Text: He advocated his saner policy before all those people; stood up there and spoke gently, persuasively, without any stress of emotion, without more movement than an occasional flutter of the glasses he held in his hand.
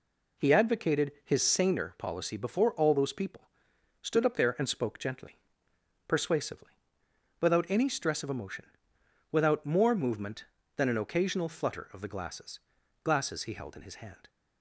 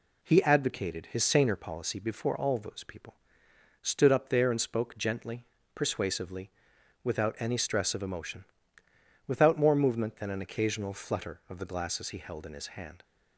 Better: second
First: says "glasses" twice; at 13.0 s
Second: none

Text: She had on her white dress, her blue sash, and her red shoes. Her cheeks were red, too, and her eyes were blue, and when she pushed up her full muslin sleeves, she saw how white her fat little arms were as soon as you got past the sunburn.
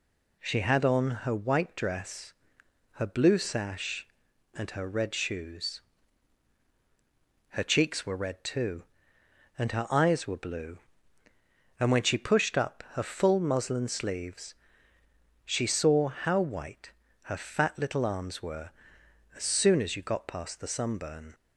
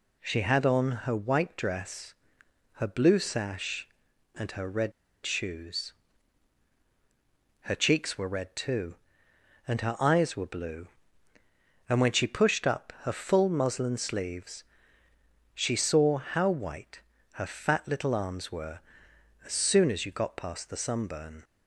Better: first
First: pauses between "white" and "her"; slight; at 16.9 s; 0.32 s long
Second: pauses between "red" and "shoes"; slight; at 4.9 s; 0.33 s long // pauses between "white" and "her"; slight; at 16.9 s; 0.32 s long

